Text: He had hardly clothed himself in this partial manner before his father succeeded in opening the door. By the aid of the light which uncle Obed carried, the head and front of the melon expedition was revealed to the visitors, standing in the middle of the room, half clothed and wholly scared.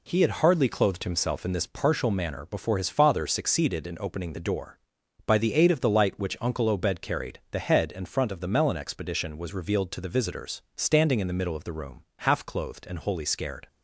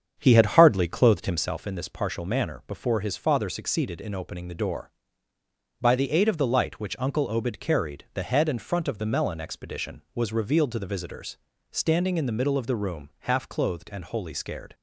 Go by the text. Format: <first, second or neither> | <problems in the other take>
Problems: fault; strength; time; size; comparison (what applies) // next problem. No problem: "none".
first | starts louder than the rest; strong; until 1.5 s; 7.5 dB